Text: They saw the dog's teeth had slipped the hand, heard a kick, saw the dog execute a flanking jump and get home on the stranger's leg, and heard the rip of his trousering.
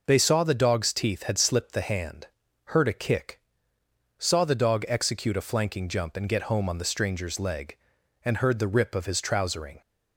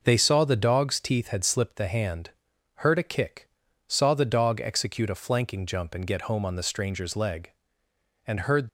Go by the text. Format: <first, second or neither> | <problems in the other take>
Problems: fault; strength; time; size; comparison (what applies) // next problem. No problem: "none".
first | stops before "the rip of his trousering"; at 8.6 s